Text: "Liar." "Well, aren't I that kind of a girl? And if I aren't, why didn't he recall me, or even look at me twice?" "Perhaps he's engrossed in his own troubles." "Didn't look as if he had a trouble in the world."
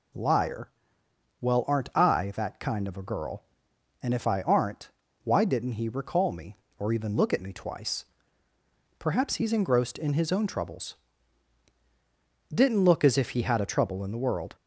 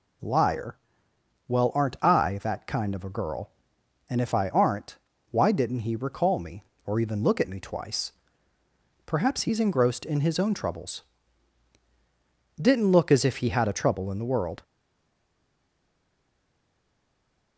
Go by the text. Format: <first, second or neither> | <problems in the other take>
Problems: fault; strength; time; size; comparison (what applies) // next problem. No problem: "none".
first | stays silent after the last word; strong; from 14.6 s on; 2.9 s long